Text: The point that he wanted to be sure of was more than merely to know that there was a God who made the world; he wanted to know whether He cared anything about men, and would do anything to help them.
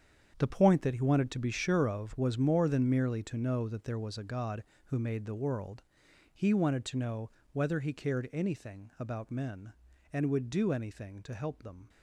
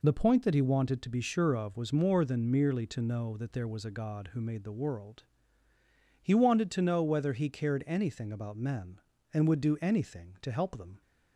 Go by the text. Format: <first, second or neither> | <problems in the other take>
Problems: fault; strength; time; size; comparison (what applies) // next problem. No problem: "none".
second | gets quieter; strong; throughout; 12.5 dB // pauses between "know" and "whether"; slight; at 7.3 s; 0.22 s long